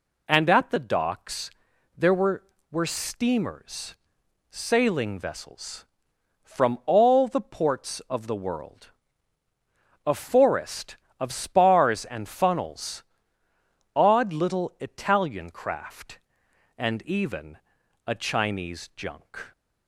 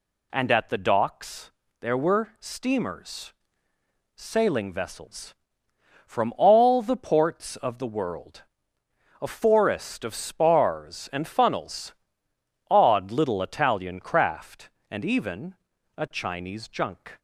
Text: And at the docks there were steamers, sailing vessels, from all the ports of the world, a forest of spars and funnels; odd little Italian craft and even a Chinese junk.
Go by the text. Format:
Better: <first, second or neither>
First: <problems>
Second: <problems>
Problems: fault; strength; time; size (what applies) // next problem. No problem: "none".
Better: second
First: pauses between "docks" and "there"; noticeable; at 1.5 s; 0.46 s long // says "were" twice; at 2.7 s // pauses between "even" and "a"; noticeable; at 17.5 s; 0.48 s long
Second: pauses between "docks" and "there"; slight; at 1.5 s; 0.30 s long // pauses between "even" and "a"; at 15.5 s; 0.42 s long